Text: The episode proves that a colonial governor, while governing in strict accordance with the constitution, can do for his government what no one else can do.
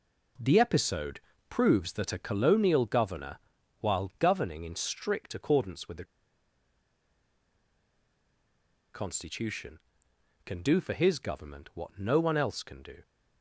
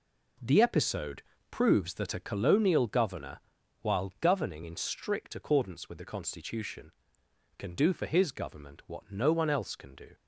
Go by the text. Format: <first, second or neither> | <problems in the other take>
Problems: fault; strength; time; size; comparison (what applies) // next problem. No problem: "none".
second | pauses between "episode" and "proves"; slight; at 1.1 s; 0.30 s long; slight in the second // pauses between "the" and "constitution"; strong; at 6.0 s; 2.8 s long